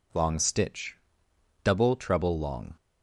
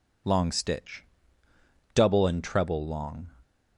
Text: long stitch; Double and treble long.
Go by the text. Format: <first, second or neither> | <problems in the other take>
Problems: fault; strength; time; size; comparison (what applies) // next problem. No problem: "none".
second | skips "and"; at 1.9 s